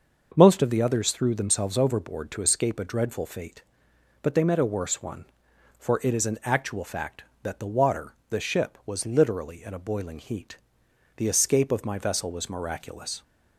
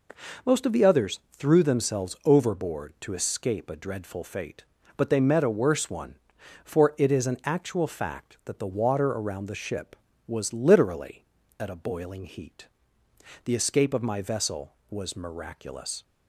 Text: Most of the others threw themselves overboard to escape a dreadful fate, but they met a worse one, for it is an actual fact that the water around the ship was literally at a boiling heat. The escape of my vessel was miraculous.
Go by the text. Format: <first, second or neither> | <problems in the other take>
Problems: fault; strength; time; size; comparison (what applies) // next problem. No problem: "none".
second | starts louder than the rest; noticeable; until 1.3 s; 6 dB // skips "around"; at 8.2 s